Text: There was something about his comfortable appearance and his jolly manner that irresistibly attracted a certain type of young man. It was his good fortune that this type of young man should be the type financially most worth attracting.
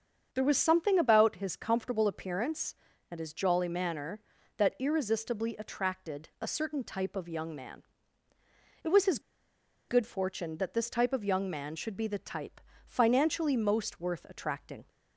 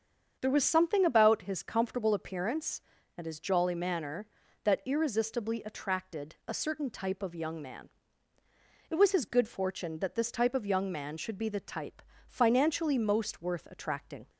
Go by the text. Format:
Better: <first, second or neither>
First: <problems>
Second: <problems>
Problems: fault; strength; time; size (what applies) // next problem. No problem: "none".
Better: second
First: starts louder than the rest; strong; until 1.3 s; 7.5 dB // pauses between "his" and "good"; noticeable; at 9.1 s; 0.69 s long // pauses between "type" and "financially"; slight; at 12.5 s; 0.26 s long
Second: starts louder than the rest; strong; until 1.4 s; 7.5 dB // pauses between "type" and "financially"; slight; at 12.0 s; 0.26 s long